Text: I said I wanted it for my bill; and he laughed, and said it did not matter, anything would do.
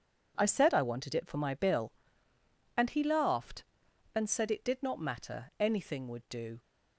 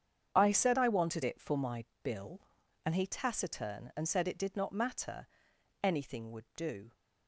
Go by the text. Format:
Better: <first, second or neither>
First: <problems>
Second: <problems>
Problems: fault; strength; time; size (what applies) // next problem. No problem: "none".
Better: first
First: none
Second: starts louder than the rest; strong; until 1.3 s; 7.5 dB // pauses between "my" and "bill"; slight; at 1.8 s; 0.20 s long // says "taciturn" for "laughed"; at 3.0 s